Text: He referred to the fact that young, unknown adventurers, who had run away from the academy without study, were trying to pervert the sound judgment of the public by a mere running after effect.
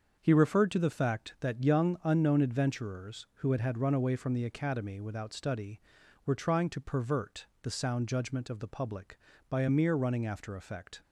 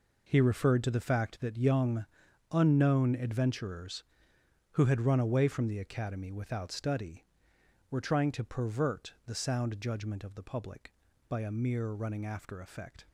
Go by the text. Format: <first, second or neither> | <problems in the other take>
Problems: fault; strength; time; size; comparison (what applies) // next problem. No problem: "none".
second | starts louder than the rest; until 1.2 s; 6.5 dB // says "had" twice; at 3.5 s // pauses between "pervert" and "the"; slight; at 7.4 s; 0.16 s long